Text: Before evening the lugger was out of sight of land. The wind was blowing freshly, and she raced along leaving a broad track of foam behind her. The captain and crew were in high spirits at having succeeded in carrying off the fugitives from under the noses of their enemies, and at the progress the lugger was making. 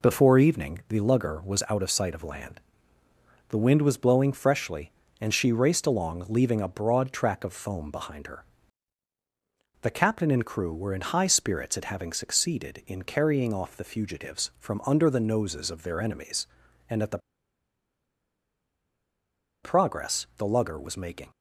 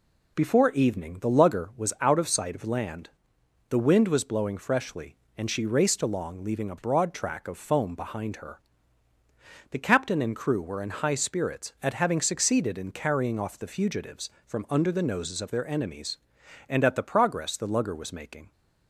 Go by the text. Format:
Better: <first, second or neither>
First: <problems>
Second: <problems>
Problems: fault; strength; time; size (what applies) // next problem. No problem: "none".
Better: second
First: pauses between "the" and "progress"; strong; at 17.1 s; 2.4 s long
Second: none